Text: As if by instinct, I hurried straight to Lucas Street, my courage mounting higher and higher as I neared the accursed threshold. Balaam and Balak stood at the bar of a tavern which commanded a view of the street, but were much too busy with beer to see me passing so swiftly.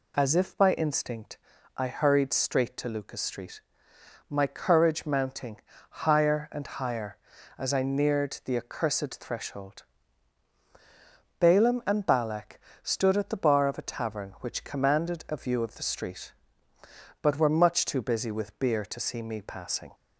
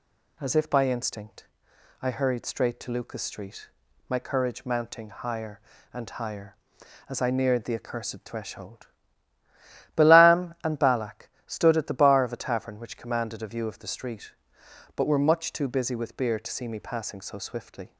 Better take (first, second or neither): second